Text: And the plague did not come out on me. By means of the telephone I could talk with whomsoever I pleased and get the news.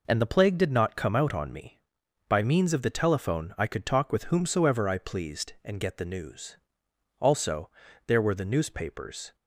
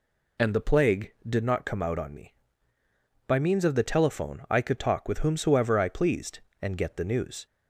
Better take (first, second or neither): second